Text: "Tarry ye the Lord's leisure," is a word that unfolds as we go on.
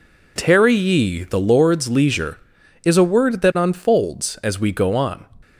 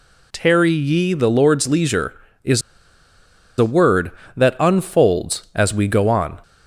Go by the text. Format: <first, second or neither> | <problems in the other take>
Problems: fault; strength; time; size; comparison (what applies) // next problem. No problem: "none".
first | pauses between "is" and "a"; noticeable; at 2.6 s; 0.97 s long